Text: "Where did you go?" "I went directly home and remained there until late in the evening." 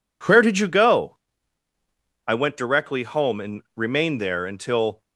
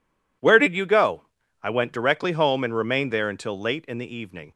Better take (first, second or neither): second